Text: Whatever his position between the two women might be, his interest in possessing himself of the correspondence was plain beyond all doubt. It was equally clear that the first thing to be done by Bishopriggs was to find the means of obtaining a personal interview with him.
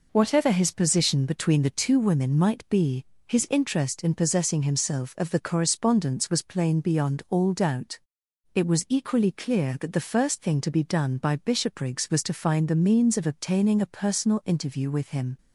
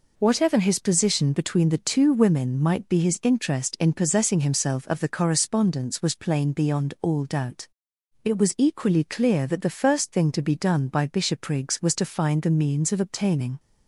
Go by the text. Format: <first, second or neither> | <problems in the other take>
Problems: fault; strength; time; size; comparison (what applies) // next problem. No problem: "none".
first | stops before "a personal interview with him"; at 13.5 s